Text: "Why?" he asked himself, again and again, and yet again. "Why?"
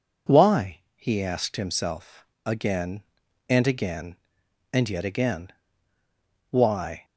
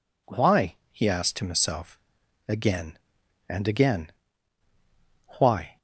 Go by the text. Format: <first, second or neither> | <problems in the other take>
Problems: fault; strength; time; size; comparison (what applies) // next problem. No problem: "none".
first | skips "and yet again"; at 4.7 s